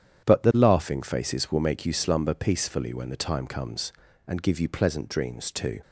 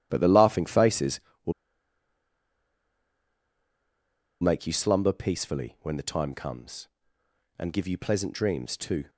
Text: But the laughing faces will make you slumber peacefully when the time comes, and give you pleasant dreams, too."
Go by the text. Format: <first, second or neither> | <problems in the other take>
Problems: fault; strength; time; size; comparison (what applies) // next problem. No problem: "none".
first | starts louder than the rest; strong; until 1.1 s; 12 dB; strong in the first // pauses between "will" and "make"; strong; at 1.5 s; 2.8 s long